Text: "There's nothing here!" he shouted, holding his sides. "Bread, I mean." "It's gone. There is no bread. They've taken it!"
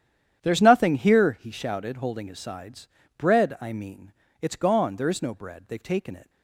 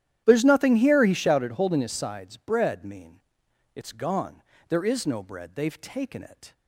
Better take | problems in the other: first | starts louder than the rest; strong; until 1.2 s; 11.5 dB; strong in the first // skips "I"; at 2.8 s

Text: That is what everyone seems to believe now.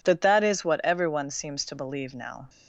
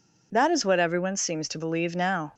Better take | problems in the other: second | says "That" twice; at 0.2 s

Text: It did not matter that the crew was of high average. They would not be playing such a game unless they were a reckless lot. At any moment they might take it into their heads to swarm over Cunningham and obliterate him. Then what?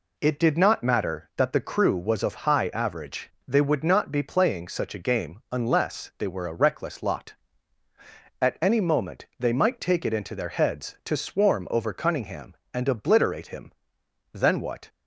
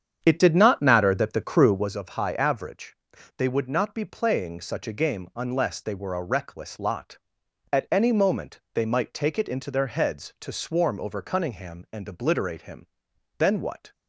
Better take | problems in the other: first | starts louder than the rest; strong; until 2.0 s; 8 dB

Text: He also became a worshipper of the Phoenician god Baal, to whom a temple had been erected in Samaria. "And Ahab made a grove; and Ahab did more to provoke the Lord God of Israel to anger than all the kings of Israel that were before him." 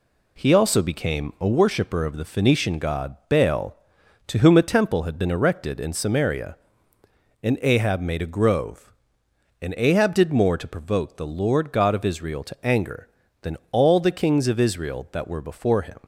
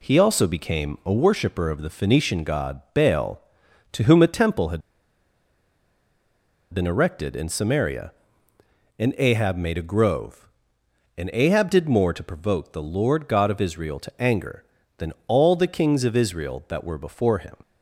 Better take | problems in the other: first | pauses between "had" and "been"; strong; at 4.8 s; 1.9 s long // pauses between "than" and "all"; slight; at 15.1 s; 0.16 s long; slight in the first

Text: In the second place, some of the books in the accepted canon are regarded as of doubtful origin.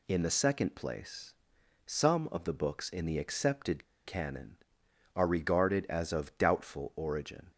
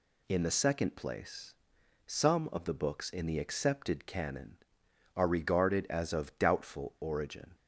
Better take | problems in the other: second | pauses between "accepted" and "canon"; slight; at 3.8 s; 0.20 s long

